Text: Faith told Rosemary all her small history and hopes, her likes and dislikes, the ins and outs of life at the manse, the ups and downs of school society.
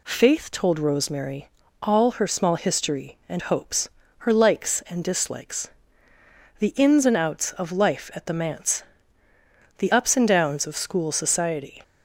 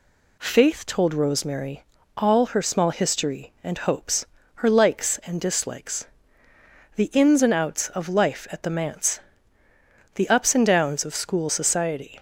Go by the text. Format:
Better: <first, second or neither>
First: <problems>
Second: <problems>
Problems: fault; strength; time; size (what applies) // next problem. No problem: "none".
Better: neither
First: pauses between "Rosemary" and "all"; slight; at 1.4 s; 0.34 s long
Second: pauses between "Rosemary" and "all"; slight; at 1.8 s; 0.34 s long